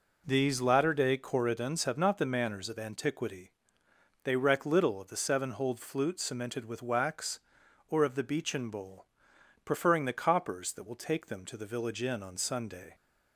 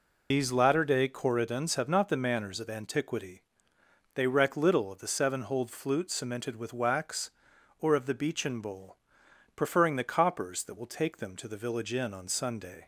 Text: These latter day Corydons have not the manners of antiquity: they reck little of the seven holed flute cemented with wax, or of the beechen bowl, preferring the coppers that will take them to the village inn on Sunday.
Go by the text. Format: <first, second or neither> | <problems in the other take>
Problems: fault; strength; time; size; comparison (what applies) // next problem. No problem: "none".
first | loses the start of "These"; at 0.3 s; 145 ms